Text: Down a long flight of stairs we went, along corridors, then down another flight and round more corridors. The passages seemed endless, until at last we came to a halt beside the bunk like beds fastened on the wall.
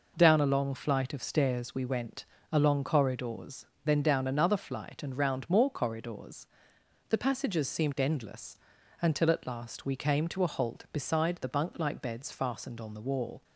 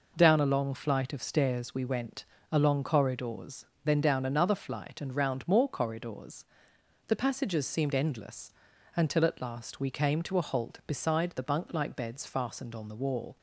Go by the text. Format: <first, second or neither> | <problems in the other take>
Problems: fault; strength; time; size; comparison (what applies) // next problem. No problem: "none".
neither | none